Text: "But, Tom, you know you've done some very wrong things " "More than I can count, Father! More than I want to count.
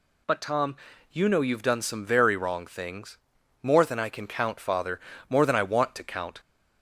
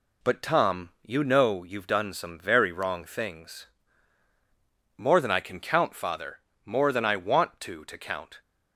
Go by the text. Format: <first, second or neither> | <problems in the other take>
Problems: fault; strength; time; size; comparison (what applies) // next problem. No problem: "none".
first | says "to" twice; at 7.8 s